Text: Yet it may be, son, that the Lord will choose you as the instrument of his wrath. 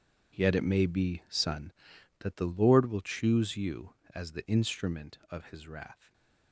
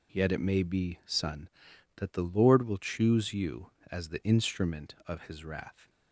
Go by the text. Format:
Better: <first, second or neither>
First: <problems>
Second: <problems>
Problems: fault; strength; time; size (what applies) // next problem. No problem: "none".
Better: second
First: gets quieter; strong; throughout; 14.5 dB // stays silent after the last word; slight; from 5.9 s on; 0.6 s long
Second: none